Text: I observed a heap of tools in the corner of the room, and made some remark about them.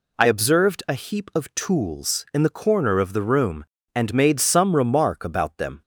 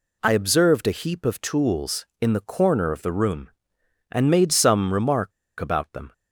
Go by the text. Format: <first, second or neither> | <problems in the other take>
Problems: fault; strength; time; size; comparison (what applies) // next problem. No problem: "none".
first | pauses between "remark" and "about"; slight; at 5.3 s; 0.27 s long